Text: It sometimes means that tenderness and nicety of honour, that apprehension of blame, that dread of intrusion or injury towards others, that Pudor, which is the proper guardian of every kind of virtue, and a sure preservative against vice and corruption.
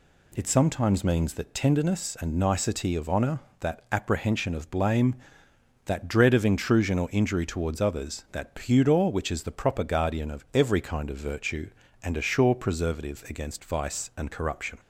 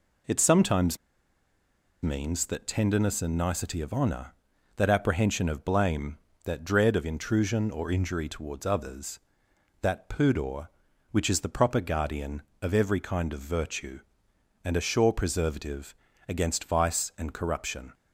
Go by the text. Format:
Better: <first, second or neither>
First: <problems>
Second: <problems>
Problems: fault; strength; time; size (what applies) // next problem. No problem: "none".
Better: first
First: none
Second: pauses between "sometimes" and "means"; at 0.9 s; 1.0 s long // pauses between "preservative" and "against"; slight; at 15.9 s; 0.34 s long